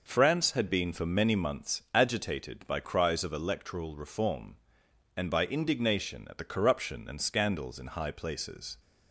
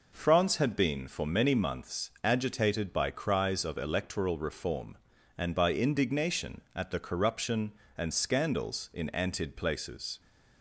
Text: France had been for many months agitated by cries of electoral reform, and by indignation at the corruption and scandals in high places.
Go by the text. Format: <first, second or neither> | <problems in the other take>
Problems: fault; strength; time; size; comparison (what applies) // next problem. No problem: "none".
first | says "antid" for "high"; at 9.1 s